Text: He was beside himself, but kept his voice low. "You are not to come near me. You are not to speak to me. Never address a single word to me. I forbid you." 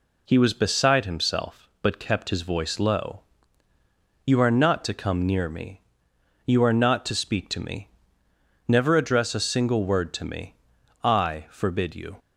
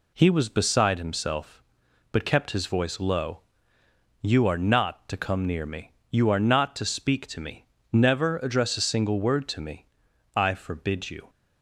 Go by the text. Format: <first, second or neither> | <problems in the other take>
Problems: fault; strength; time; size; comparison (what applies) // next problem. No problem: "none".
neither | none